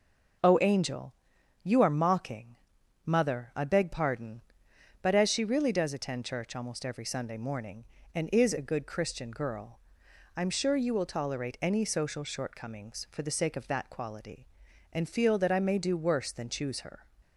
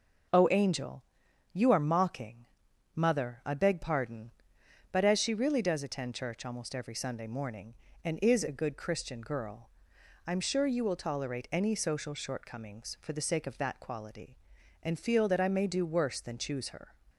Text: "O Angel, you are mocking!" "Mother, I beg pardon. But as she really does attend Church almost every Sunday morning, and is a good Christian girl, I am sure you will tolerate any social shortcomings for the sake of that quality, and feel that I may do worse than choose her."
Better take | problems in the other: neither | none

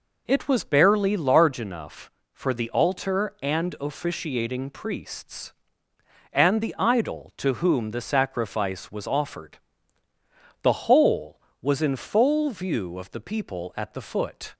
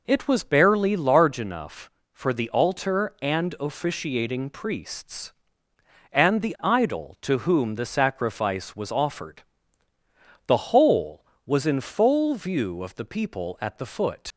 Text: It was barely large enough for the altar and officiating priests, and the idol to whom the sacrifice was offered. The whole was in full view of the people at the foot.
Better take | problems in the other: first | leaves "foot" unfinished; at 14.3 s; 80 ms

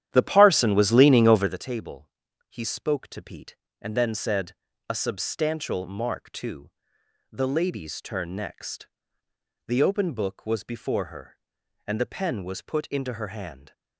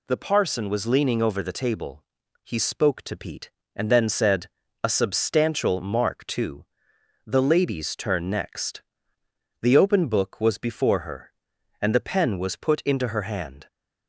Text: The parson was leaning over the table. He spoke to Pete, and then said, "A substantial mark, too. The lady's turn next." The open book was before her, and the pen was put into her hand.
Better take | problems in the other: second | starts louder than the rest; strong; until 1.6 s; 11 dB

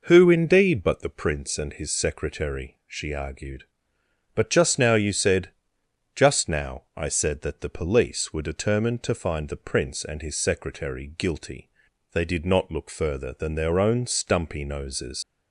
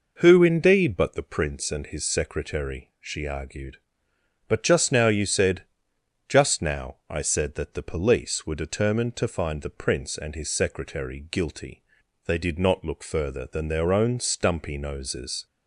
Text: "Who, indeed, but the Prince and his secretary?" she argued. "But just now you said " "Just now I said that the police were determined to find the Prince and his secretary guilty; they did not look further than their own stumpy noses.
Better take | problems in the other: second | leaves "noses" unfinished; at 15.2 s; 100 ms

